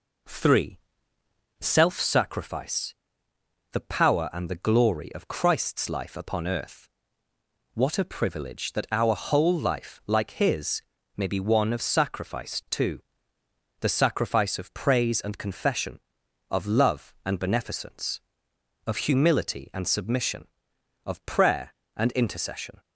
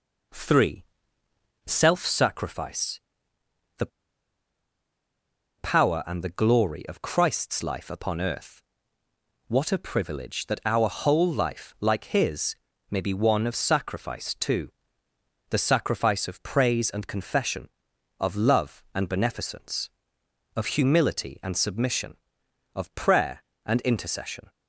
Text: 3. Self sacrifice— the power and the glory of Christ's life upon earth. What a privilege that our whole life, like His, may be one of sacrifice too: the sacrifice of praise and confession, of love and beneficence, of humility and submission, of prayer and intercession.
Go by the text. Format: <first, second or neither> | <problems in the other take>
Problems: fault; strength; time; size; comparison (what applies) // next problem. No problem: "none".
first | pauses between "the" and "power"; strong; at 3.8 s; 1.7 s long